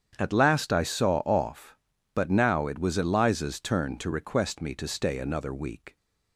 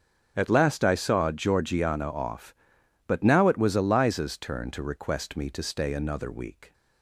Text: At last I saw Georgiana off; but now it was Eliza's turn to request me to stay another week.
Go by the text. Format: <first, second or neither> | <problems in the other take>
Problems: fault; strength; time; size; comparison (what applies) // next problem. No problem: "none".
second | starts louder than the rest; strong; until 1.2 s; 8 dB; strong in the second // skips "Georgiana"; at 1.2 s